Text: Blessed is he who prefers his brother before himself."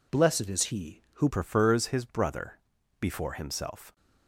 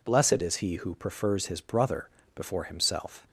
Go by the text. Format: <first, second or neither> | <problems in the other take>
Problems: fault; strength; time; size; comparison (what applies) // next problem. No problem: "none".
second | changes voice at "prefers"; from 1.2 s on; 2.7 s long // pauses between "brother" and "before"; at 2.5 s; 0.42 s long; slight in the second